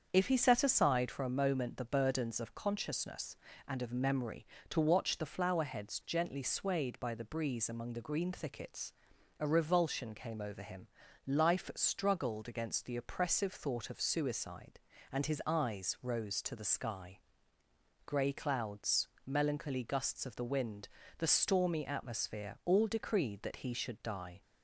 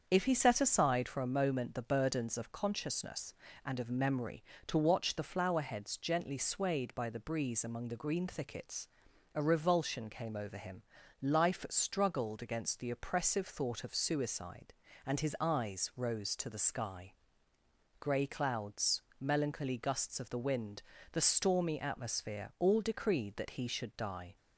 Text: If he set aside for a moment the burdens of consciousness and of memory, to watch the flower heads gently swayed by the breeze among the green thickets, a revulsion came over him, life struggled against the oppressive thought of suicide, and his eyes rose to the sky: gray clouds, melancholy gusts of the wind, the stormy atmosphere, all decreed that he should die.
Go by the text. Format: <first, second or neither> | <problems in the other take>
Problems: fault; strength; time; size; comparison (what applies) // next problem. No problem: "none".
neither | starts louder than the rest; the same in both